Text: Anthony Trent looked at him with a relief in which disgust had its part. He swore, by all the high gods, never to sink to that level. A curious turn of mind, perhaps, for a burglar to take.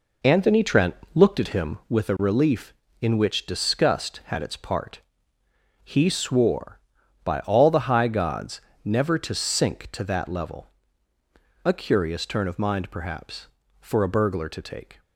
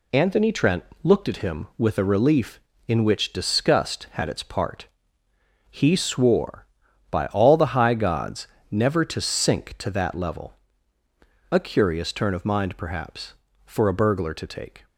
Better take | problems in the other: second | starts louder than the rest; noticeable; until 2.0 s; 4 dB // pauses between "Trent" and "looked"; slight; at 0.9 s; 0.20 s long; slight in the second

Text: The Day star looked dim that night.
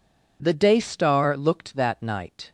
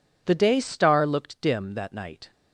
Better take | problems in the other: second | skips "dim"; at 1.7 s

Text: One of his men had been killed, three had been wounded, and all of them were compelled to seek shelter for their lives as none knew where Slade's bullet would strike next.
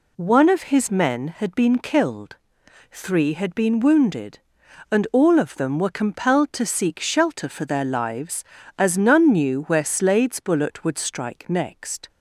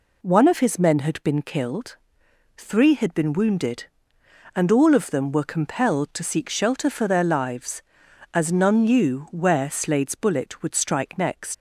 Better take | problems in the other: first | leaves "next" unfinished; at 11.5 s; 120 ms

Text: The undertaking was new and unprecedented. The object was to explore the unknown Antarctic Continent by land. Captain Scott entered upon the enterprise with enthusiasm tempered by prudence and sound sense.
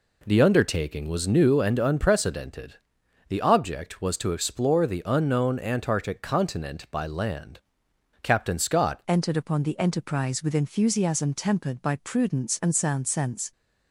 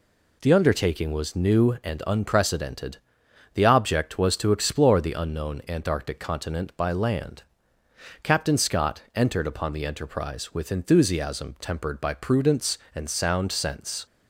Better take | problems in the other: second | changes voice at "entered"; from 9.0 s on; 4.5 s long

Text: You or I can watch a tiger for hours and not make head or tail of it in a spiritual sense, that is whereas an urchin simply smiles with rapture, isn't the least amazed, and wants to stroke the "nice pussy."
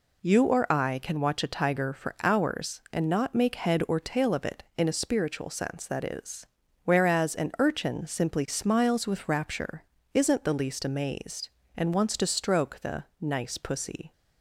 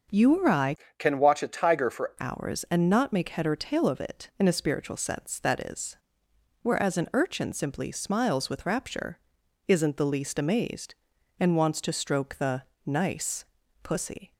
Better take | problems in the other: first | starts louder than the rest; until 1.3 s; 6.5 dB // changes voice from "can" to "for"; from 0.9 to 2.1 s; 1.2 s long // pauses between "is" and "whereas"; noticeable; at 5.9 s; 0.66 s long; also in the first // pauses between "the" and "nice"; slight; at 12.6 s; 0.24 s long; slight in the first // pauses between "nice" and "pussy"; at 13.4 s; 0.40 s long

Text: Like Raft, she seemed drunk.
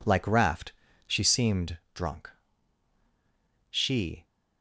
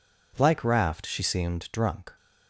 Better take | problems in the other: second | pauses between "seemed" and "drunk"; slight; at 1.7 s; 0.16 s long // goes on to say "She"; from 3.6 s on; 0.54 s long

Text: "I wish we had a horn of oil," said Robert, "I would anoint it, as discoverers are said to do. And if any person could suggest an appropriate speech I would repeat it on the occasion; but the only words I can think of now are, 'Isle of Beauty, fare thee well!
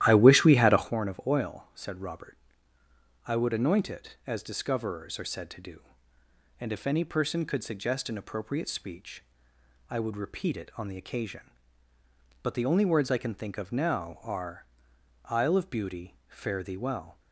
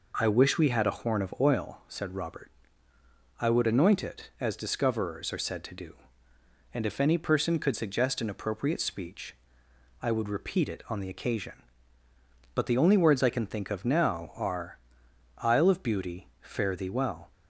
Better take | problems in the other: second | starts louder than the rest; strong; until 1.0 s; 13 dB // pauses between "speech" and "I"; noticeable; at 9.2 s; 0.70 s long; noticeable in the second

